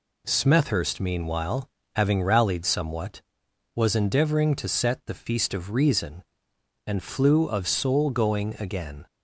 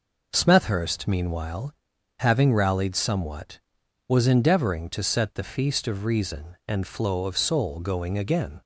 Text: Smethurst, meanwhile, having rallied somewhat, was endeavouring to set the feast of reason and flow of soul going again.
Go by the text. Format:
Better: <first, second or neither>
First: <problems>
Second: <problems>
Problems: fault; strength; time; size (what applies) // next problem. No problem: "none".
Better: second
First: says "flew" for "flow"; at 7.0 s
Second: none